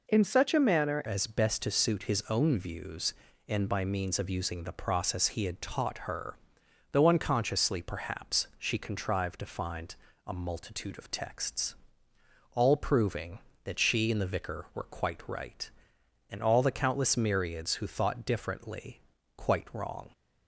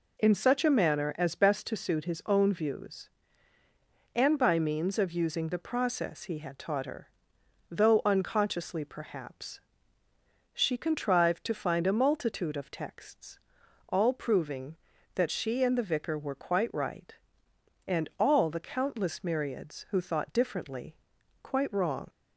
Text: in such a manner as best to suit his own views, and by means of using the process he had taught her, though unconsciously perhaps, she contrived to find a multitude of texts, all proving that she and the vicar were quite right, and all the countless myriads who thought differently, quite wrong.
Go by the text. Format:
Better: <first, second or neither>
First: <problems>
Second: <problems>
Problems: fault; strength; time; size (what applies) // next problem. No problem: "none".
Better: second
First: changes voice at "as"; from 1.0 s on; 19.1 s long // pauses between "find" and "a"; slight; at 9.9 s; 0.32 s long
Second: none